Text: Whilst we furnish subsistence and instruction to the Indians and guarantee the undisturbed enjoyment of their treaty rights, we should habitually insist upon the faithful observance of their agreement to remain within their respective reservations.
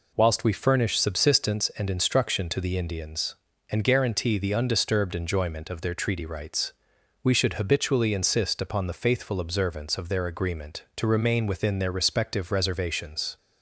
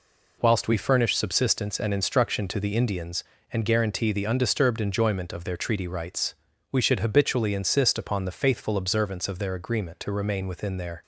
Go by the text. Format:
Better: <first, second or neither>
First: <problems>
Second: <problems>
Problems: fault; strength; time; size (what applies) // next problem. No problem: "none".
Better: first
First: none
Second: stops before "respective reservations"; at 11.0 s